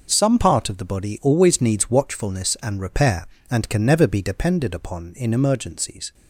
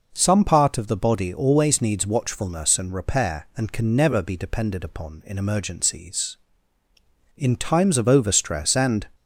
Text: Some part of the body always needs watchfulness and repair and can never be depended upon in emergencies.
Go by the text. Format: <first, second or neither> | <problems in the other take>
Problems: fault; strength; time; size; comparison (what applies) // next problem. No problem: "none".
first | goes on to say "In times of overstress and"; strong; from 7.3 s on; 1.7 s long